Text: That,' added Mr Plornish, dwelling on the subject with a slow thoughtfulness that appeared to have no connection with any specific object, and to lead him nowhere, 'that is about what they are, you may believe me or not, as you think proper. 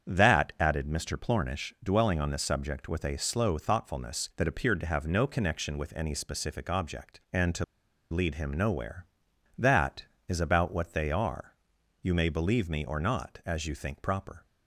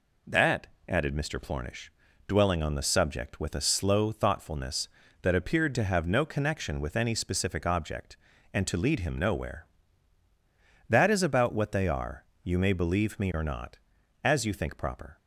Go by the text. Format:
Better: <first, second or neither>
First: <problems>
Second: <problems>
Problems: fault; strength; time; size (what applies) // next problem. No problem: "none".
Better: second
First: starts louder than the rest; strong; until 1.1 s; 7.5 dB // pauses between "to" and "lead"; noticeable; at 7.6 s; 0.47 s long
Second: none